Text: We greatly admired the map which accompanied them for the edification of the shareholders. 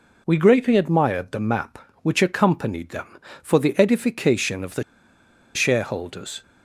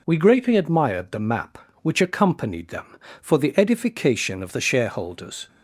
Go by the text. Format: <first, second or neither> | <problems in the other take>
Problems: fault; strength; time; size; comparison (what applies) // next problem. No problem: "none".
second | pauses between "the" and "shareholders"; noticeable; at 4.8 s; 0.72 s long